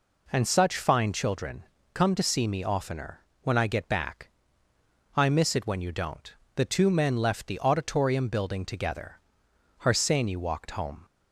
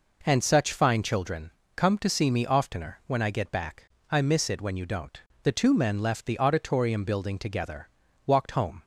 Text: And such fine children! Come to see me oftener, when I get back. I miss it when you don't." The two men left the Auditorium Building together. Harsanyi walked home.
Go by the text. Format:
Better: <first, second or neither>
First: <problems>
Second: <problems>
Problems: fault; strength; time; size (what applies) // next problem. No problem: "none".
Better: first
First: none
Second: skips "Harsanyi"; at 8.0 s